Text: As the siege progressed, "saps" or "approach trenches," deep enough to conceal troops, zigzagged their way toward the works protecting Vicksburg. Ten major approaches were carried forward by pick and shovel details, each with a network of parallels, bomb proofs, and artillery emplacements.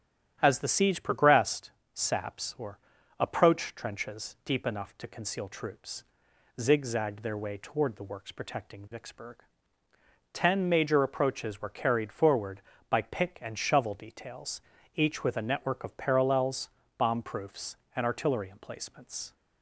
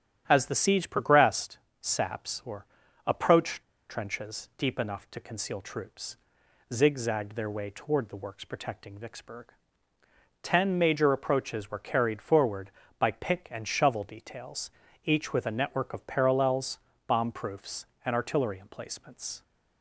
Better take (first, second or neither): first